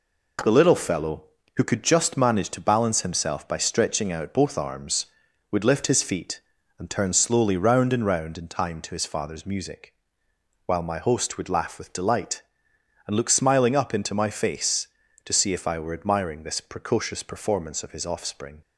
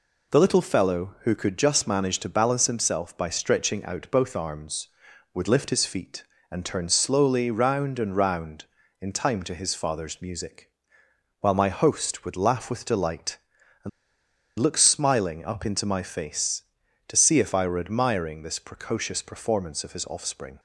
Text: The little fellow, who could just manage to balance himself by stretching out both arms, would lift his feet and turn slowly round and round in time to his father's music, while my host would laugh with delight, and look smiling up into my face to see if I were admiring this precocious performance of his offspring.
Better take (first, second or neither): first